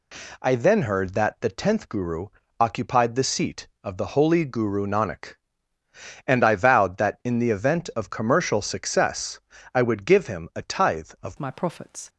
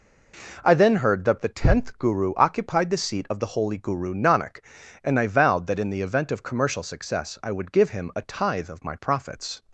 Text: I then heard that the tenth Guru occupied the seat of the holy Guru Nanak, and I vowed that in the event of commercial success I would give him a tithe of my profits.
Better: second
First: pauses between "Guru" and "occupied"; slight; at 2.2 s; 0.34 s long // pauses between "success" and "I"; slight; at 9.4 s; 0.32 s long // changes voice at "my"; from 11.3 s on; 0.7 s long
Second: none

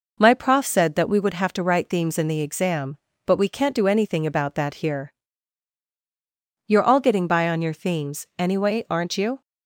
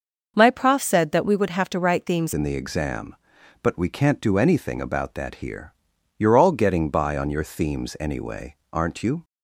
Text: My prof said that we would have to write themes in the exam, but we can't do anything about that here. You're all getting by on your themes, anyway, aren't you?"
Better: first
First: none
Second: starts louder than the rest; until 1.3 s; 6 dB // changes voice at "in"; from 2.3 s on; 6.9 s long

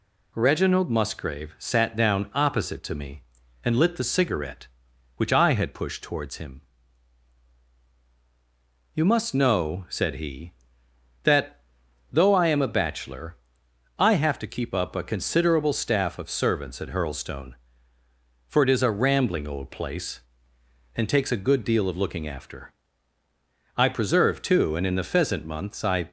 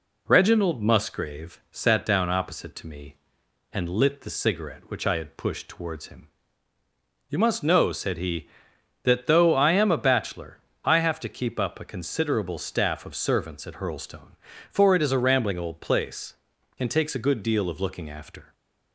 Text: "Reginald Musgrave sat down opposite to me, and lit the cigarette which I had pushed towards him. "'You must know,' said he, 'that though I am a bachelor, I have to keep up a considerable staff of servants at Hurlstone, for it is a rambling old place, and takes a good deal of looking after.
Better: second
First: pauses between "that" and "though"; noticeable; at 11.5 s; 0.52 s long // goes on to say "I preserve too and in the pheasant months I"; strong; from 23.7 s on; 2.3 s long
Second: none

